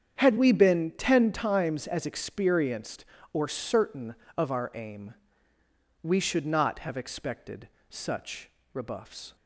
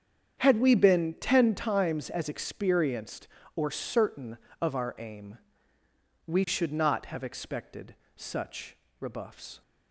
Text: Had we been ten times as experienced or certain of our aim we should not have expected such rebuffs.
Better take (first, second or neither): neither